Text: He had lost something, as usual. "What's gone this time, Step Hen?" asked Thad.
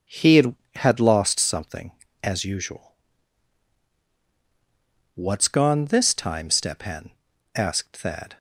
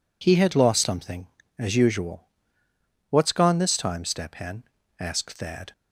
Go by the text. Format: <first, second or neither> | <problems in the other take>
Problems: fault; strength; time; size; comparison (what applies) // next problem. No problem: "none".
second | starts louder than the rest; until 1.3 s; 6.5 dB // says "had" twice; at 0.7 s